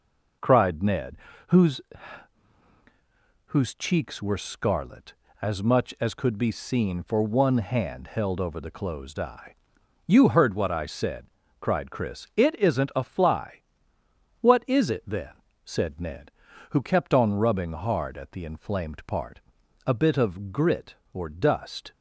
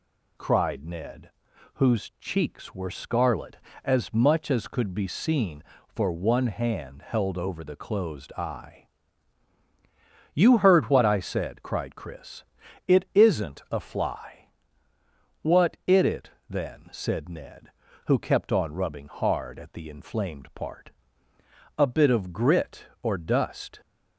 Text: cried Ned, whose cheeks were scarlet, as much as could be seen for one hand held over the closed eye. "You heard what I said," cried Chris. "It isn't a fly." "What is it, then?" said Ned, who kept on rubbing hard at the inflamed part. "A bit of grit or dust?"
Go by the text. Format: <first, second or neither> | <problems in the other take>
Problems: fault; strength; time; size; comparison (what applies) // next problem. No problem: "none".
second | says "whose" twice; at 3.4 s